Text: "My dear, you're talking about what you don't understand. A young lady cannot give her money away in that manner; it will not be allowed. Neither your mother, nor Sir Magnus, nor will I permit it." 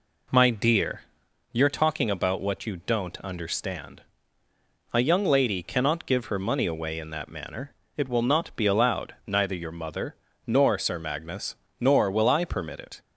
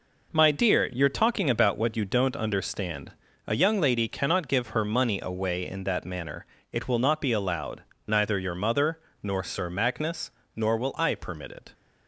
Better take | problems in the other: neither | none

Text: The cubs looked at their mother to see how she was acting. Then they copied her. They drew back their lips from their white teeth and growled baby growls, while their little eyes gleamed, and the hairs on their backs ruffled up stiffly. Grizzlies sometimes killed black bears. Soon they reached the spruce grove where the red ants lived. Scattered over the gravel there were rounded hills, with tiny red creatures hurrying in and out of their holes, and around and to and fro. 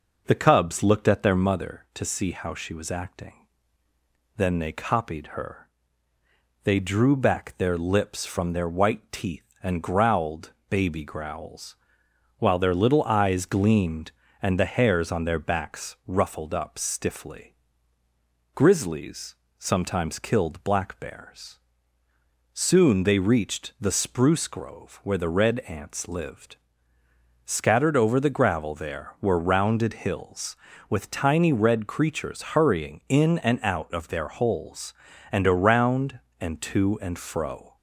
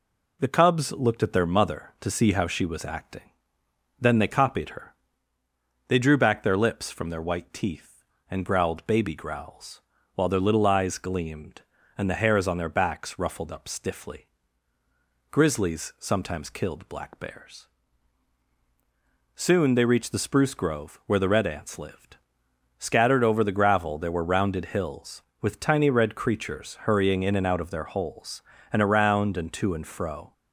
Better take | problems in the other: second | starts louder than the rest; noticeable; until 1.5 s; 5.5 dB // pauses between "growled" and "baby"; slight; at 10.5 s; 0.16 s long // pauses between "Grizzlies" and "sometimes"; slight; at 19.3 s; 0.24 s long

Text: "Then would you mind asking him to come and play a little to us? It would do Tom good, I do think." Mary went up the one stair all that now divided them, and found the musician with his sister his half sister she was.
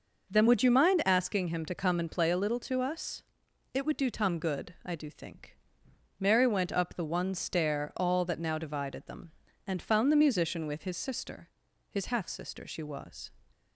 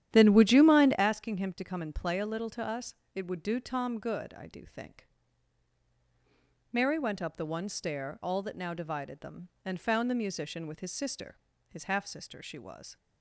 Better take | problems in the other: first | starts louder than the rest; strong; until 1.0 s; 11 dB // pauses between "sister" and "his"; slight; at 11.3 s; 0.32 s long; also in the first

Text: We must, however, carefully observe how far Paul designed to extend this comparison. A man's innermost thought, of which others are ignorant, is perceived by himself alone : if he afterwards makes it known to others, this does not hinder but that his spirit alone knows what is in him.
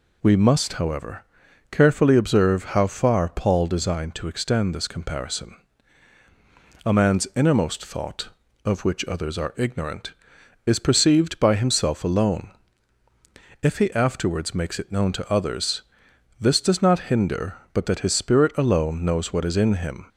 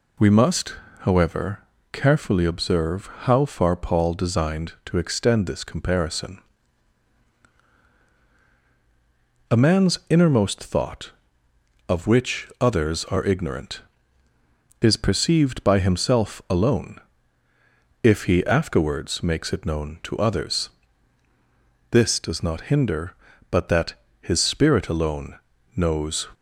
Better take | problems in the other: first | pauses between "observe" and "how"; slight; at 3.0 s; 0.18 s long // pauses between "that" and "his"; slight; at 23.9 s; 0.26 s long // pauses between "alone" and "knows"; at 25.3 s; 0.38 s long // stops before "what is in him"; at 26.3 s

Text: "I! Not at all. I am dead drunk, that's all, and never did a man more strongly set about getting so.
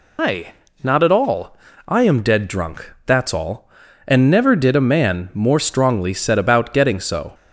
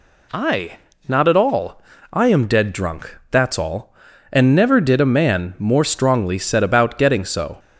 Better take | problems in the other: second | loses the start of "I"; at 0.1 s; 130 ms

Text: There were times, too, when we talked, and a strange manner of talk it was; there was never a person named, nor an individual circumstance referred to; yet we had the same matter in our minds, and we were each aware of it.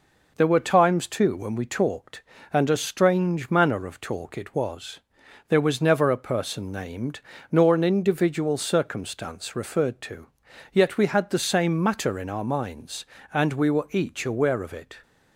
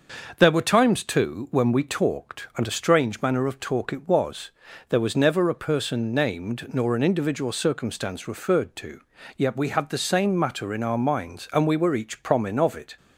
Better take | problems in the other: first | starts louder than the rest; until 1.3 s; 6 dB // says "promin" for "aware"; at 12.2 s

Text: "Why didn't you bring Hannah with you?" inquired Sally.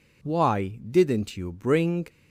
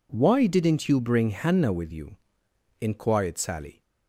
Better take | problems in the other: second | stops before "Hannah with you inquired Sally"; at 2.0 s

